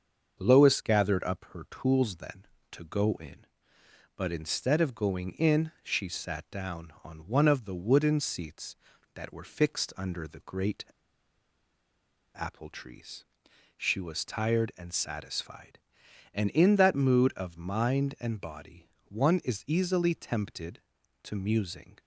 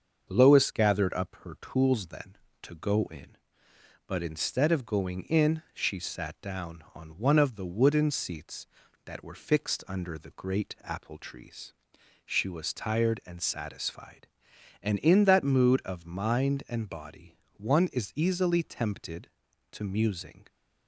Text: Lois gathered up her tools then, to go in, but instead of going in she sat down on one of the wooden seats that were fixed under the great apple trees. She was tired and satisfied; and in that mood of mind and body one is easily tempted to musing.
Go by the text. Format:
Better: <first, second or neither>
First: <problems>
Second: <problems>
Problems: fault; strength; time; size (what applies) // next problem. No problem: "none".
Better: second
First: starts louder than the rest; until 1.4 s; 6.5 dB // pauses between "great" and "apple"; strong; at 10.8 s; 1.5 s long // pauses between "body" and "one"; slight; at 18.8 s; 0.20 s long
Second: starts louder than the rest; until 1.3 s; 6.5 dB // pauses between "body" and "one"; slight; at 17.3 s; 0.20 s long